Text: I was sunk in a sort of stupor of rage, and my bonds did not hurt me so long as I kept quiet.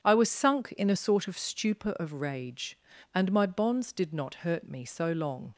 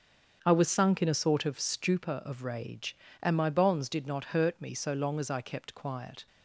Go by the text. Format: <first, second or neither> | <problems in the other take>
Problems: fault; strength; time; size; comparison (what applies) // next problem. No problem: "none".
second | starts louder than the rest; strong; until 1.0 s; 8 dB; strong in the second // stops before "as I kept quiet"; at 5.5 s